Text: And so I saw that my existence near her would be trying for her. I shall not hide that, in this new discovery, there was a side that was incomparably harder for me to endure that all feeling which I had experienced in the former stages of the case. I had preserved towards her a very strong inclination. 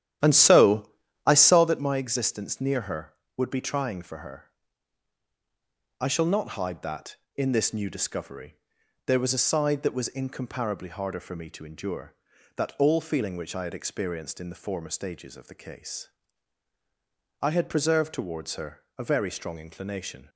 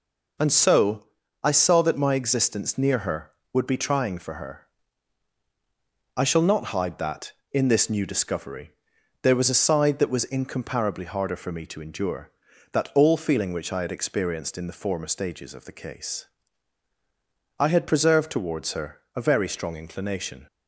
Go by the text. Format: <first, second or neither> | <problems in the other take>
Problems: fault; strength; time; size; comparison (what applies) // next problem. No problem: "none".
second | starts louder than the rest; strong; until 1.8 s; 11.5 dB // pauses between "so" and "I"; slight; at 0.9 s; 0.36 s long; slight in the second // pauses between "her" and "a"; slight; at 18.8 s; 0.16 s long; slight in the second